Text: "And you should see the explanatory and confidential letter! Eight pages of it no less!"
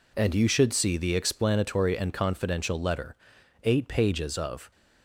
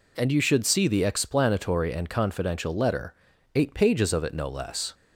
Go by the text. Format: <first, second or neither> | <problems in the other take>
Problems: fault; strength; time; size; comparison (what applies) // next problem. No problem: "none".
second | stops before "it no less"; at 4.7 s